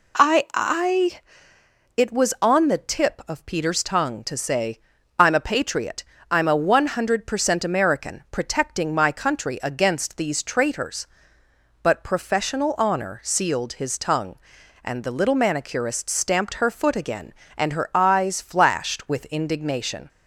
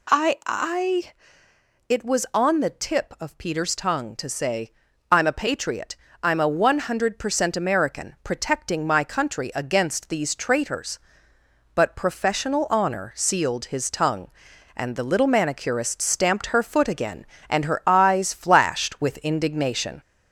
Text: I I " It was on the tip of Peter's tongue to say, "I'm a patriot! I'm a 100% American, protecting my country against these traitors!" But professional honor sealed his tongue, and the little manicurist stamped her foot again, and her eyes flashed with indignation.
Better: first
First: none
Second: gets louder; noticeable; throughout; 5.5 dB

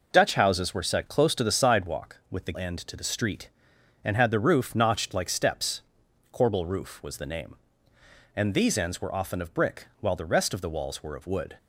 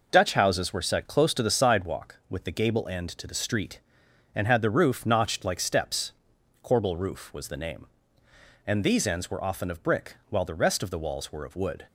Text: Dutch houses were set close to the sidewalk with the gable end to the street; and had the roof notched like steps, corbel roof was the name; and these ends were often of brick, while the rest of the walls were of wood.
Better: second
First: skips "gable"; at 2.5 s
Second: none

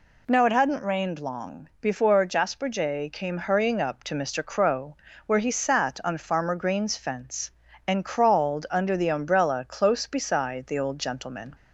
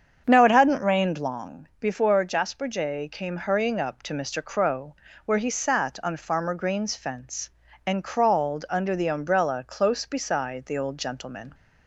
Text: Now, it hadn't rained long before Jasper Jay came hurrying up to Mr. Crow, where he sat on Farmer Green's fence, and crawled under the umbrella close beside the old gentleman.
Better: first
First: none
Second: starts louder than the rest; strong; until 1.4 s; 7.5 dB

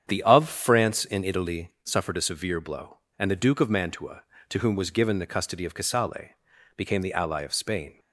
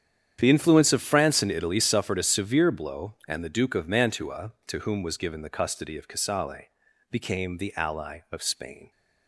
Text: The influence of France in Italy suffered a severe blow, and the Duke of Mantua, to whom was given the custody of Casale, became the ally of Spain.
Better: second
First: starts louder than the rest; strong; until 1.0 s; 8.5 dB // skips "influence"; at 0.2 s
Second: starts louder than the rest; strong; until 1.4 s; 9 dB

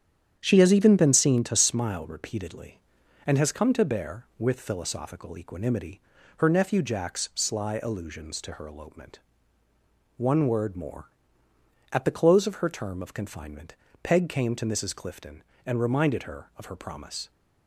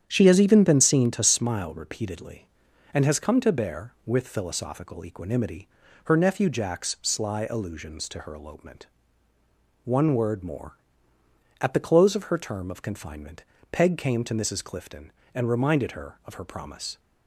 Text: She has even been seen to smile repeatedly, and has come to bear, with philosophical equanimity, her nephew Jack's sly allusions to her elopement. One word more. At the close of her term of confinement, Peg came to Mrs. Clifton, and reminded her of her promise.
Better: neither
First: starts louder than the rest; strong; until 1.4 s; 9 dB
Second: starts louder than the rest; strong; until 1.0 s; 9.5 dB

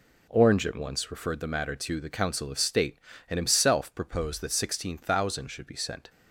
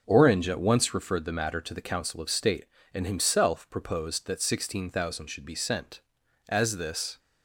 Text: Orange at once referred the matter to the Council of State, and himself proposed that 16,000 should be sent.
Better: first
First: none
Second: goes on to say "As this"; noticeable; from 6.4 s on; 0.70 s long

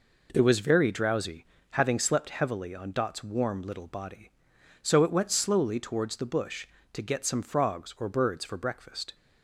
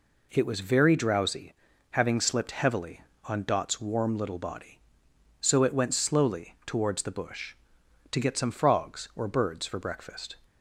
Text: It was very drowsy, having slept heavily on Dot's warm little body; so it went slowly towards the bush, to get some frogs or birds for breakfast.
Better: first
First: none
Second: says "slipped" for "slept"; at 2.1 s

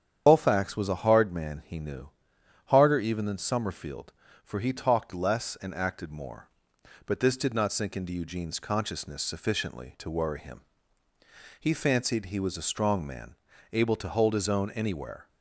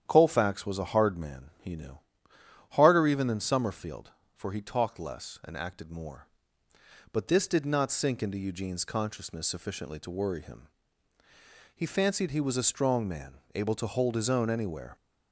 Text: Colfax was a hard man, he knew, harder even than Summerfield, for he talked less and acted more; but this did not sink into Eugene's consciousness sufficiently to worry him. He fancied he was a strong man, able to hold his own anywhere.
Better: second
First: loses the start of "Colfax"; at 0.2 s; 110 ms // starts louder than the rest; strong; until 1.2 s; 8.5 dB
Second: starts louder than the rest; strong; until 1.0 s; 9.5 dB

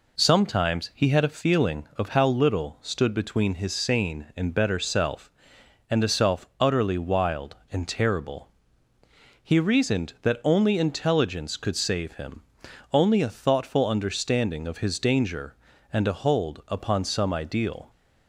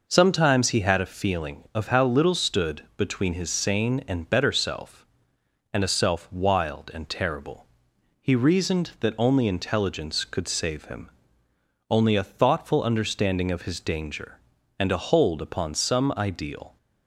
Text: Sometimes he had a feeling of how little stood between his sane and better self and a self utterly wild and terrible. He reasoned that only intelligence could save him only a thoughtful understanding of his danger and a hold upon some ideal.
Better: first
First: pauses between "him" and "only"; noticeable; at 12.4 s; 0.50 s long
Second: skips "utterly"; at 6.3 s // pauses between "him" and "only"; noticeable; at 11.1 s; 0.78 s long

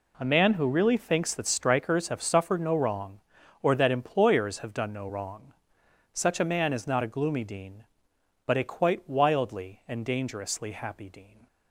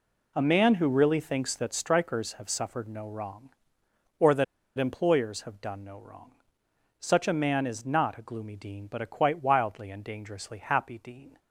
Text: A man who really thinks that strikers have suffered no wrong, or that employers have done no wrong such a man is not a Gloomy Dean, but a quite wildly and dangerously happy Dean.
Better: first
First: pauses between "wrong" and "such"; noticeable; at 5.5 s; 0.64 s long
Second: pauses between "that" and "employers"; slight; at 4.4 s; 0.33 s long // pauses between "wrong" and "such"; noticeable; at 6.3 s; 0.70 s long

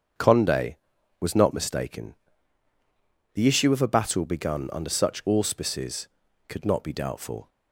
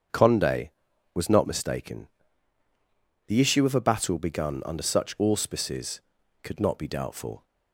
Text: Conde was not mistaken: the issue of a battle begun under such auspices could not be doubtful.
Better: neither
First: starts louder than the rest; until 1.6 s; 7 dB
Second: starts louder than the rest; until 1.5 s; 7 dB

